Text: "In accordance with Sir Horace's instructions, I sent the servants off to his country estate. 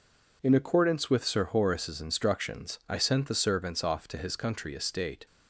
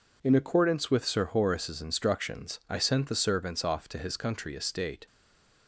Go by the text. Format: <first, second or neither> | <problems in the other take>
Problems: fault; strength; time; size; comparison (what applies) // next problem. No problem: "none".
first | stays silent after the last word; slight; from 5.0 s on; 0.6 s long